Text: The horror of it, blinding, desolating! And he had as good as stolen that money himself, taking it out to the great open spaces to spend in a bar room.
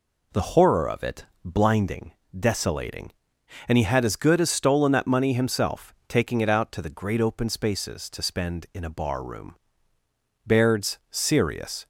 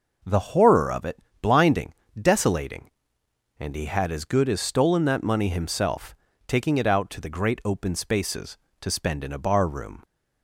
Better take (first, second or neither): second